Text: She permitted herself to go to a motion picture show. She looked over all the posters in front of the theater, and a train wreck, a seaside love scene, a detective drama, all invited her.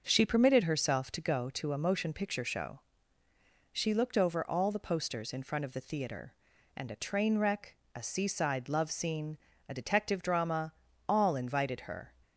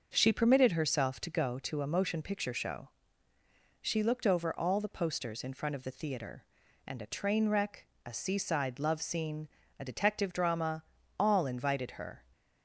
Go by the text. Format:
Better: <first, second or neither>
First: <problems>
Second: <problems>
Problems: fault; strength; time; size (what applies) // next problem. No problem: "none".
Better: neither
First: starts louder than the rest; until 1.0 s; 6.5 dB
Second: starts louder than the rest; until 1.1 s; 6.5 dB